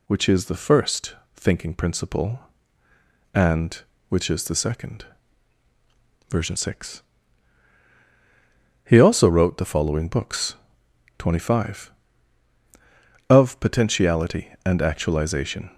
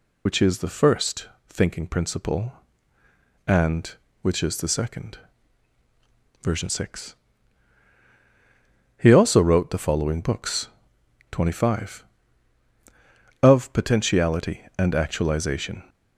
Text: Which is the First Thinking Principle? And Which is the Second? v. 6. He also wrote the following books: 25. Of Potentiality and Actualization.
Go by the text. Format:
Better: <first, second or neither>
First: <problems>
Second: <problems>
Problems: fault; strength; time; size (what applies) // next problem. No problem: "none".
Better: first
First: pauses between "First" and "Thinking"; slight; at 1.1 s; 0.18 s long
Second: loses the start of "Which"; at 0.2 s; 45 ms // pauses between "First" and "Thinking"; slight; at 1.2 s; 0.18 s long